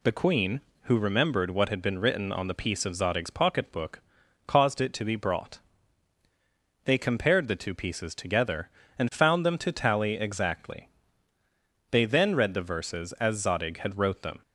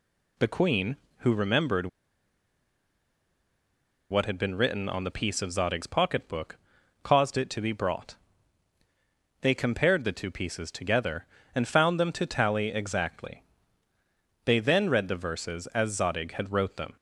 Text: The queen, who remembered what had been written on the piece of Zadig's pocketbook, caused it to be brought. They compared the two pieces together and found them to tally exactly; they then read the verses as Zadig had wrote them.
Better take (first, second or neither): first